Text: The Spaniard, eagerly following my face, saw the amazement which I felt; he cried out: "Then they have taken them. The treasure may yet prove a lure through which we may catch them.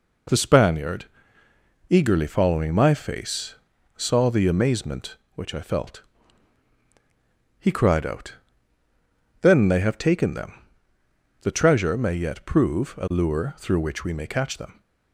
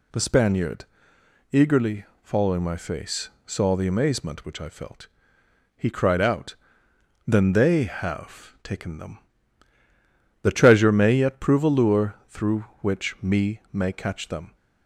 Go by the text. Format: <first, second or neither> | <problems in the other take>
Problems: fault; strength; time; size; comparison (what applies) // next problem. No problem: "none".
first | pauses between "eagerly" and "following"; slight; at 2.0 s; 0.20 s long // says "me" for "we"; at 13.2 s